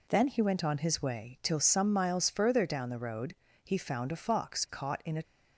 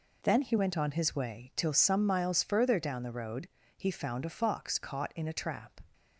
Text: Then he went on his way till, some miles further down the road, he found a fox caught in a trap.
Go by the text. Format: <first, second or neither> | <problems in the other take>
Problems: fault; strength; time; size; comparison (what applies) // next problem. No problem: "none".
second | stops before "trap"; at 5.2 s